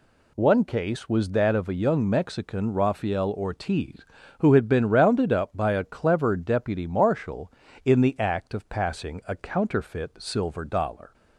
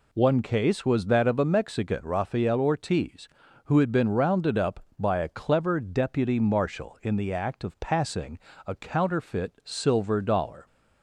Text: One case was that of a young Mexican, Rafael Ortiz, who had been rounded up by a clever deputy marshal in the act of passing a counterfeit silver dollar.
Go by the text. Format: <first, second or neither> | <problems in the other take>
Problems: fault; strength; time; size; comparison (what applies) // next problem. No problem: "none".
first | skips "young"; at 1.4 s // pauses between "passing" and "a"; slight; at 8.3 s; 0.26 s long